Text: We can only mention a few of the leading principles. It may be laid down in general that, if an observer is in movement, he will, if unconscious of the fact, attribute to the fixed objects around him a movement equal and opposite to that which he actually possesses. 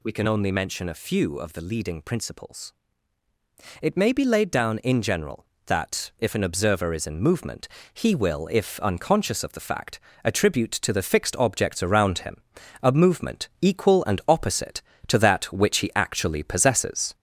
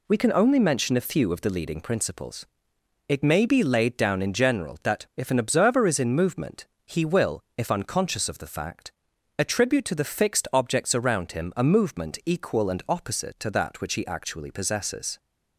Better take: second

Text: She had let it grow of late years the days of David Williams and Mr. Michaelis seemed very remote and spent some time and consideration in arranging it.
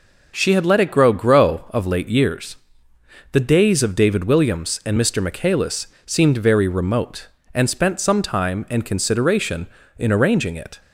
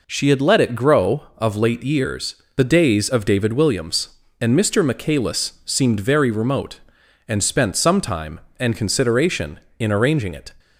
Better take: second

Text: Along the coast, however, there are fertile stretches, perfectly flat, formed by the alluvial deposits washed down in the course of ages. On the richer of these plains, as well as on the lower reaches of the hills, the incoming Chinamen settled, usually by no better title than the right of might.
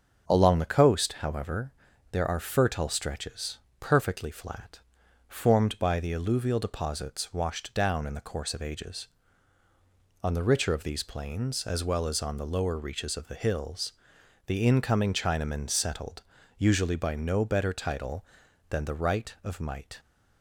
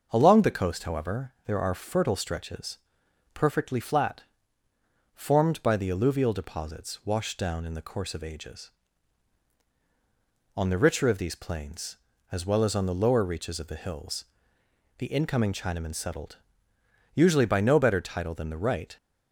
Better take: first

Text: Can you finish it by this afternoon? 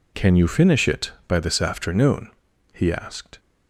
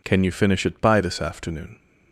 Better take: second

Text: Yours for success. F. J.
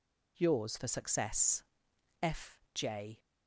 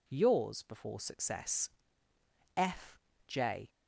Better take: first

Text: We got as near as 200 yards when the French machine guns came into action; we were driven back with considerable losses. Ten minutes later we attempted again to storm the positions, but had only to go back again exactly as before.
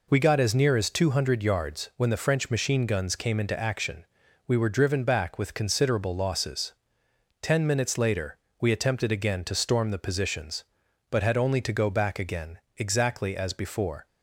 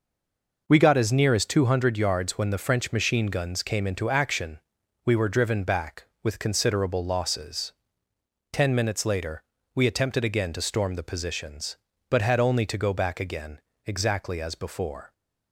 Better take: first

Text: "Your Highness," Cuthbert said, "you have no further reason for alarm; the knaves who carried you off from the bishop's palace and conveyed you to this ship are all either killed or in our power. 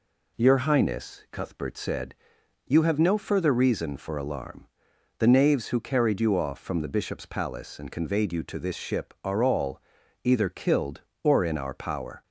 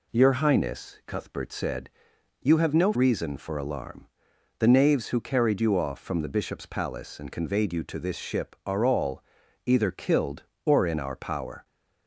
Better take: first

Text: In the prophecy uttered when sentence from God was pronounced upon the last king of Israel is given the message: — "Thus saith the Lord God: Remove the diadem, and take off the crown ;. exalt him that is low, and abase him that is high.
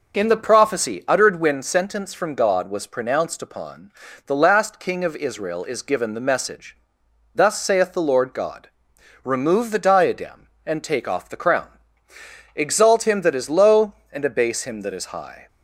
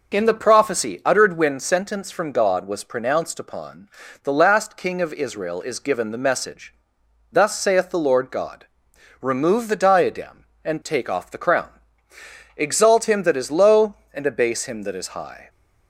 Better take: neither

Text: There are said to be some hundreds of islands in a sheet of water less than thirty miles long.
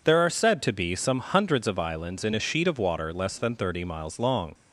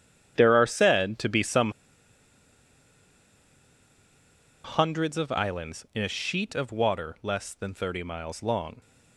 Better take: first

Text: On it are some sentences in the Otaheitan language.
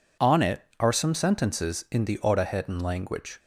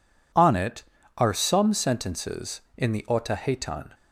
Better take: first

